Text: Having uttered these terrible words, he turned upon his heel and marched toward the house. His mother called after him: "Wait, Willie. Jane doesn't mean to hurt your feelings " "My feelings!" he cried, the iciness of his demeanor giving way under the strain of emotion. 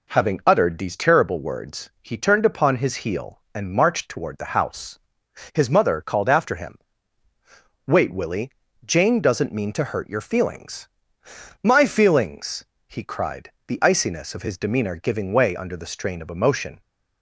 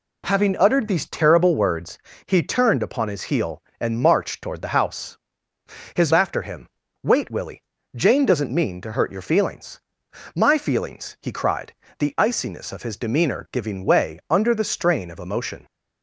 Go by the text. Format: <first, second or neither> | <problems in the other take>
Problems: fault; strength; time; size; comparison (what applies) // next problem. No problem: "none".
first | skips "mother called"; at 6.1 s